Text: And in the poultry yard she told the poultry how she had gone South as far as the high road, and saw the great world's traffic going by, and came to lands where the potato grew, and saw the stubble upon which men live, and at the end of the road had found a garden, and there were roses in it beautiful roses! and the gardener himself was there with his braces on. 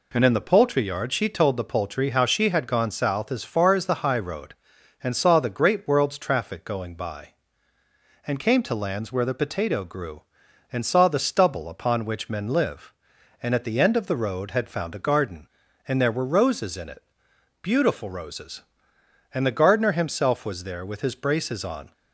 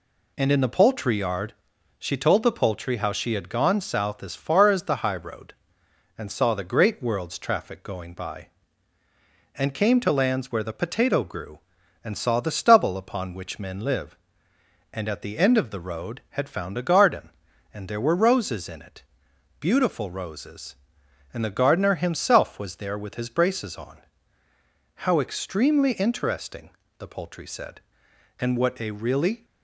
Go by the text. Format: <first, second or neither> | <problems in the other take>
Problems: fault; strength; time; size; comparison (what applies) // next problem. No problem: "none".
first | pauses between "yard" and "she"; noticeable; at 1.5 s; 0.46 s long // pauses between "it" and "beautiful"; noticeable; at 19.0 s; 0.56 s long; noticeable in the first // goes on to say "How extremely interesting the poultry said and what a really"; strong; from 25.0 s on; 4.4 s long